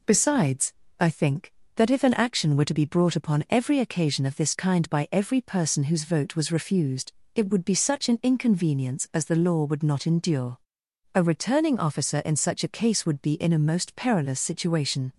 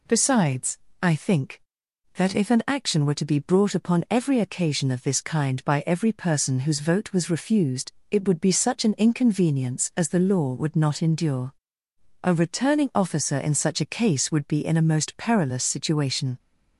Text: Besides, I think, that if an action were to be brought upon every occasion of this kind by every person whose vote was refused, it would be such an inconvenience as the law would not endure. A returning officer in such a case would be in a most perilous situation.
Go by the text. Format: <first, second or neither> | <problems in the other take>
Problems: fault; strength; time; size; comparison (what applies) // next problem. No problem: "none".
neither | none